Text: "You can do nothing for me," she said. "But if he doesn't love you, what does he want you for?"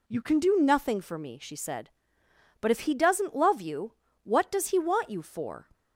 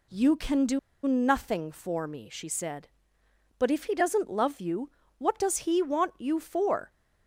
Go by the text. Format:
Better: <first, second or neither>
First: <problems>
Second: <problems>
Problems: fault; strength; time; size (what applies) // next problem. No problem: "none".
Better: first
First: none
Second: pauses between "do" and "nothing"; slight; at 0.7 s; 0.26 s long